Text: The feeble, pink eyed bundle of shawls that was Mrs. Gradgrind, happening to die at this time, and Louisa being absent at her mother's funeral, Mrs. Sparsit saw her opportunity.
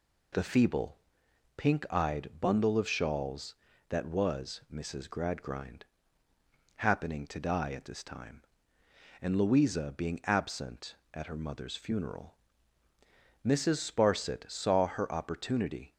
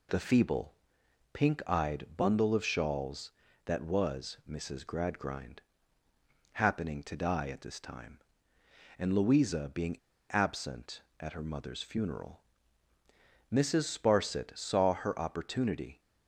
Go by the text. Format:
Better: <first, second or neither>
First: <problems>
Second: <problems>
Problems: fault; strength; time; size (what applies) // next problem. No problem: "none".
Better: first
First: none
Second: pauses between "being" and "absent"; slight; at 9.9 s; 0.31 s long